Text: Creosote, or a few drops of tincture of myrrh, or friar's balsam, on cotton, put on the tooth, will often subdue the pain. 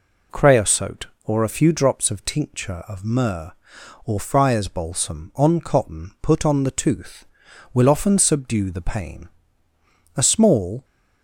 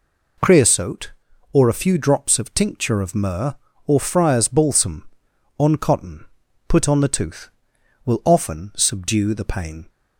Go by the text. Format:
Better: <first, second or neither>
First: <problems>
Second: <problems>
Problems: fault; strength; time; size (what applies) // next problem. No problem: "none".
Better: second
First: goes on to say "A small"; noticeable; from 10.1 s on; 0.68 s long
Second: none